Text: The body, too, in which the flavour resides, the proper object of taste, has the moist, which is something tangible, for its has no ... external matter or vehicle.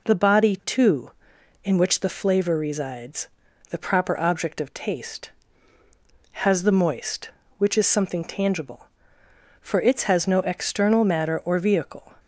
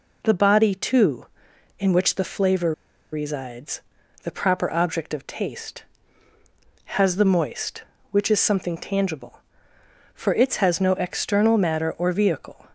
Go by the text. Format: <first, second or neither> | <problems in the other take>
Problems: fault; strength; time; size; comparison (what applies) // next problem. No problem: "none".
first | pauses between "flavour" and "resides"; at 2.7 s; 0.40 s long